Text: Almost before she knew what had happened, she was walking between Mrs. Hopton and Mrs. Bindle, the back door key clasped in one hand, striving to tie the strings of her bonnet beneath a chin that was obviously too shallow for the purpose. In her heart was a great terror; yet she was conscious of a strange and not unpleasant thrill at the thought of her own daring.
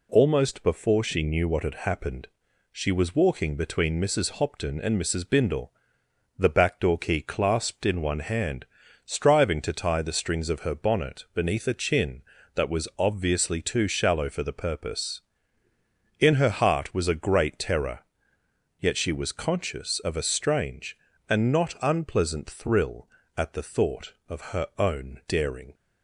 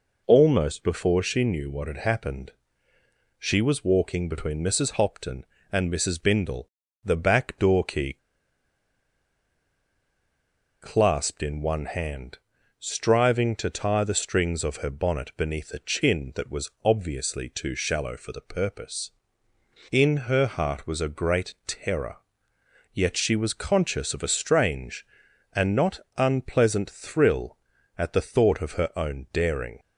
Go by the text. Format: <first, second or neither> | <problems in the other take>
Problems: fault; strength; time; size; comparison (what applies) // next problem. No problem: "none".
first | pauses between "key" and "clasped"; strong; at 8.1 s; 2.6 s long // pauses between "not" and "unpleasant"; slight; at 26.0 s; 0.16 s long